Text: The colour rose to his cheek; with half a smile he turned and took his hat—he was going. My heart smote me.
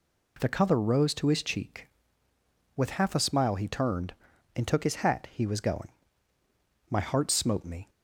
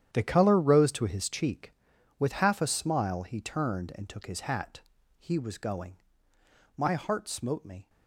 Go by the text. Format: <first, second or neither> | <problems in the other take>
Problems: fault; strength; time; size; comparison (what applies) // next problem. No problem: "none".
first | gets quieter; strong; throughout; 14.5 dB